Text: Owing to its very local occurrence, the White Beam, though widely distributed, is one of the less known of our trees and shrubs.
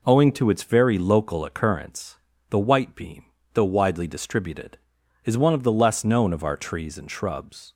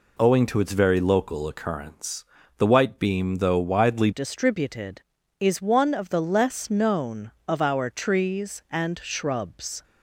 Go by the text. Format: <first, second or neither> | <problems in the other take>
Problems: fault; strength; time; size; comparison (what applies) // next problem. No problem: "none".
first | changes voice at "distributed"; from 4.1 s on; 5.7 s long